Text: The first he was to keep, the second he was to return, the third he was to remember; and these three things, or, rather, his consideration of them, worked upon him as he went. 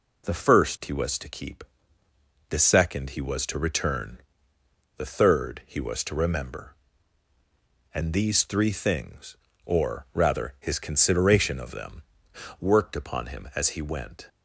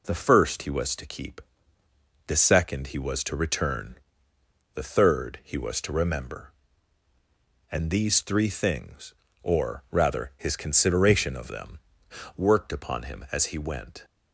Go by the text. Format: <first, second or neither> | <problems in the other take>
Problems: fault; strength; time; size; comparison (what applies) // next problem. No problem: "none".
neither | none